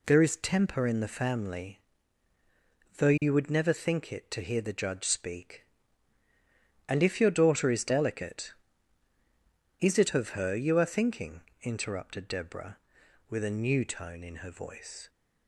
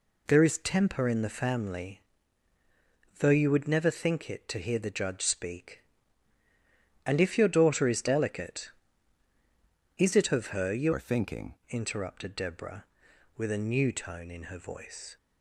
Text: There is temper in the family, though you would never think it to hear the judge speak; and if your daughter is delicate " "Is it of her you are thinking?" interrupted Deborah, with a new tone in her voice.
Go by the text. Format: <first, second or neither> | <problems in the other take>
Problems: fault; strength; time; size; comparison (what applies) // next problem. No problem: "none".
first | changes voice from "are" to "thinking"; from 10.9 to 11.5 s; 0.6 s long